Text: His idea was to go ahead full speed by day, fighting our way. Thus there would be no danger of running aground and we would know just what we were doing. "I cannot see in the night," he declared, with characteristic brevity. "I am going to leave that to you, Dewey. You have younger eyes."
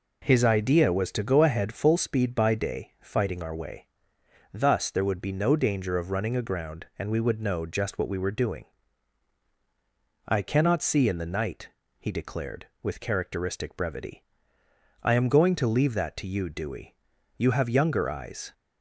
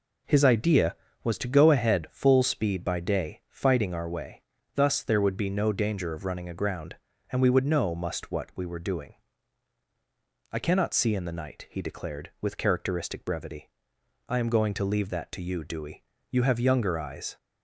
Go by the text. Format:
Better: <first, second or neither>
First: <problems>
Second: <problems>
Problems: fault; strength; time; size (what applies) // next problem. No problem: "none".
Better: first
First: none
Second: says "must" for "just"; at 7.9 s